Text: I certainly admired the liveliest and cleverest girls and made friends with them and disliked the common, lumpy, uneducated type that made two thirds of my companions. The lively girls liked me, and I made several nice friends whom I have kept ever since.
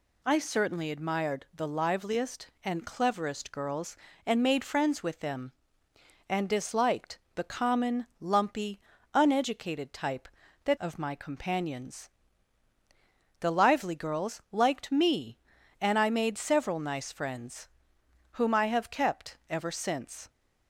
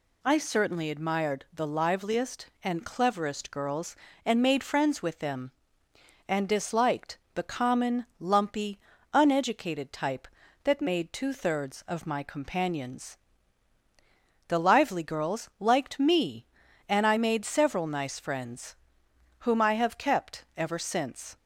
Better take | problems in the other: second | pauses between "disliked" and "the"; slight; at 7.1 s; 0.16 s long; slight in the second // skips "made two thirds"; at 10.7 s // pauses between "friends" and "whom"; noticeable; at 17.6 s; 0.64 s long; noticeable in the second

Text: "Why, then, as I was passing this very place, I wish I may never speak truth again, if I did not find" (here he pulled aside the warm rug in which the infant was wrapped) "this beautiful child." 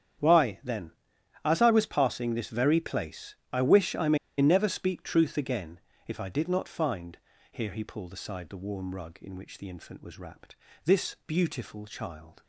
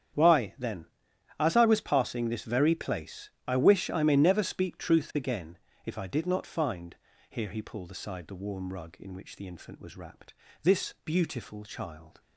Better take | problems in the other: second | starts louder than the rest; strong; until 1.8 s; 9 dB; strong in the second // pauses between "may" and "never"; slight; at 4.1 s; 0.23 s long

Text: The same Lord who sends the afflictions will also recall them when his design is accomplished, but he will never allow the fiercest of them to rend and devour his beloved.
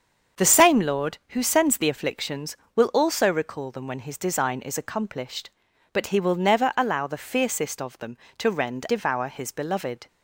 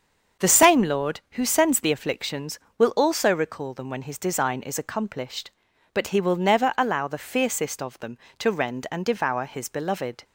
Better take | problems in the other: second | starts louder than the rest; until 1.4 s; 7 dB; also in the second // skips "and"; at 8.8 s

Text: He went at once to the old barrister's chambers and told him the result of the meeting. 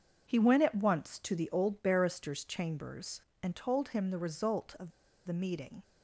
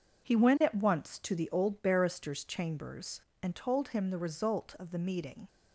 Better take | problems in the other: second | pauses between "of" and "the"; slight; at 4.9 s; 0.34 s long

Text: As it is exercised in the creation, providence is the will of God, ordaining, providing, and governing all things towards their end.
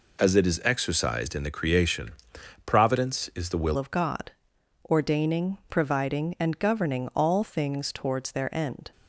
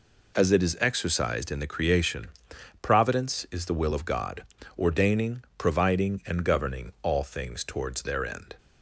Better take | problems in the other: second | changes voice at "of"; from 3.7 s on; 5.2 s long

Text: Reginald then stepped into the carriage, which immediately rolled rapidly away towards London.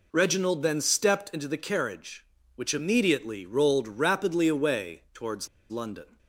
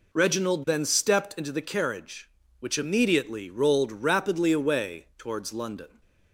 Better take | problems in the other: second | pauses between "towards" and "London"; slight; at 5.4 s; 0.21 s long

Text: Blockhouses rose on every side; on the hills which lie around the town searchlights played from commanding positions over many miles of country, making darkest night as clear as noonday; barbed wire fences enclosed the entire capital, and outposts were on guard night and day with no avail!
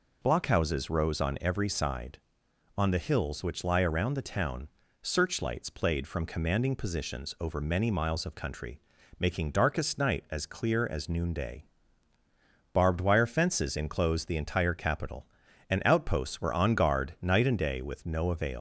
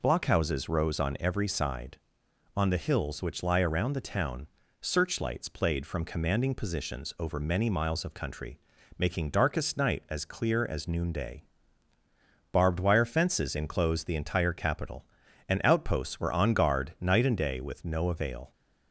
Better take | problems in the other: second | pauses between "town" and "searchlights"; slight; at 4.6 s; 0.36 s long; slight in the second // leaves "avail" unfinished; at 18.5 s; 130 ms

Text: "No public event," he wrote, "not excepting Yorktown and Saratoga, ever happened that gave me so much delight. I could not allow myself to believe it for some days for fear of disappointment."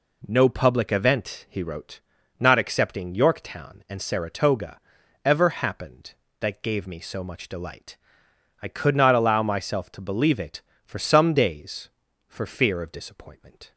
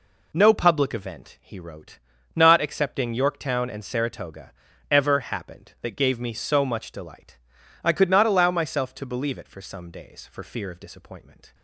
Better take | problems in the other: neither | none

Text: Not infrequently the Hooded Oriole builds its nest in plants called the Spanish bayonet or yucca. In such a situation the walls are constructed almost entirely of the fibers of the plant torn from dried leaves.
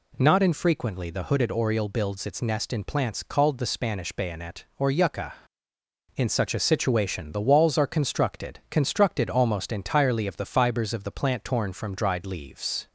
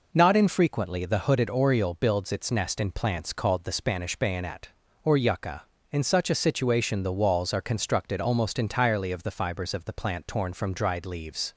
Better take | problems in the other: second | says "constructed" twice; at 8.6 s

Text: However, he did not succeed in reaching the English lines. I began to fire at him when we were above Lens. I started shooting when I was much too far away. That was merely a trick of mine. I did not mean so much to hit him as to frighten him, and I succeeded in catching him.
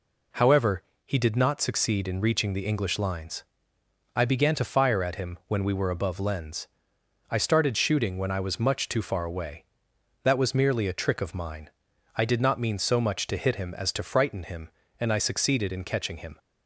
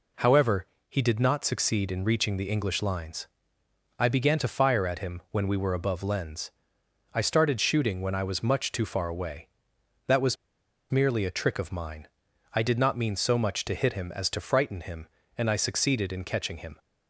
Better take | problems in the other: first | pauses between "was" and "merely"; noticeable; at 10.3 s; 0.56 s long

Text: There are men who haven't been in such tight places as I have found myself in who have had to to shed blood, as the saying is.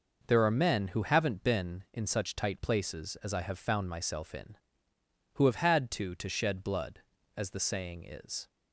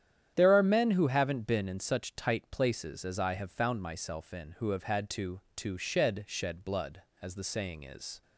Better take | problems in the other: first | starts louder than the rest; strong; until 1.3 s; 10 dB // says "shed" twice; at 6.2 s

